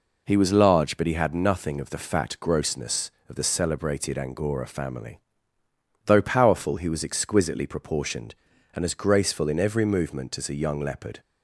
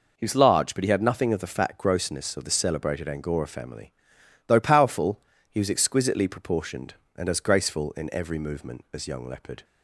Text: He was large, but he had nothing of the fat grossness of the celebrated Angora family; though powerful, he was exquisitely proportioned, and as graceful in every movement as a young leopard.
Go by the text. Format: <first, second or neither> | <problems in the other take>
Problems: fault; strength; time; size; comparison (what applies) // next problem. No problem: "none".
first | skips "a"; at 9.0 s